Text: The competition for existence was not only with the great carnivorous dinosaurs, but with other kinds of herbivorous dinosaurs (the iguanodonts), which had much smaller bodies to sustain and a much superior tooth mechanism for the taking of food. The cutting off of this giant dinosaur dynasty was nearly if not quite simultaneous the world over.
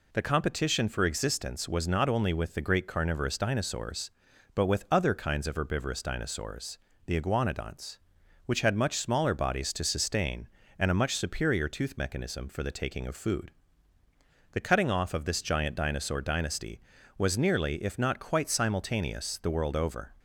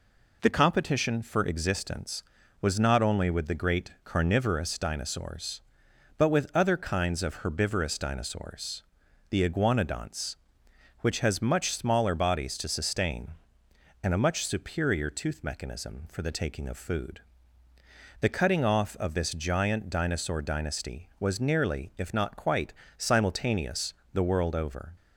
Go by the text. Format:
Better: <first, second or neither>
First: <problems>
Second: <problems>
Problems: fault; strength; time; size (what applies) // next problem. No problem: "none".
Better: first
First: none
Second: says "has" for "had"; at 11.1 s // pauses between "quite" and "simultaneous"; slight; at 22.7 s; 0.24 s long // pauses between "simultaneous" and "the"; slight; at 23.9 s; 0.22 s long